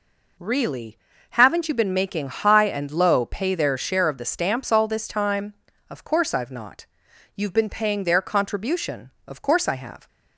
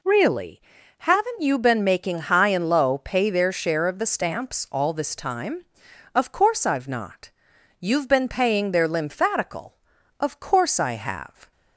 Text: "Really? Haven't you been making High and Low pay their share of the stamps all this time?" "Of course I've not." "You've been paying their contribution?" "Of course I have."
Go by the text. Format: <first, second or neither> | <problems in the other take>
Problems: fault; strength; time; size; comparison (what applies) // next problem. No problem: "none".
first | says "lymphatical" for "contribution"; at 8.8 s